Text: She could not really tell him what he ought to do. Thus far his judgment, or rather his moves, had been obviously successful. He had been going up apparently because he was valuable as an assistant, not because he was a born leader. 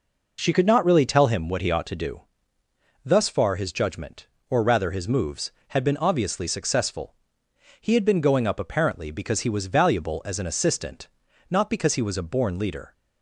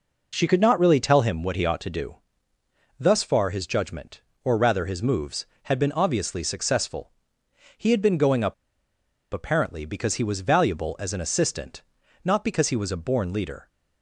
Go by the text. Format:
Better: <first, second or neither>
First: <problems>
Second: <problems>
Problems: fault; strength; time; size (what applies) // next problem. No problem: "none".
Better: first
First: none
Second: pauses between "up" and "apparently"; noticeable; at 8.5 s; 0.79 s long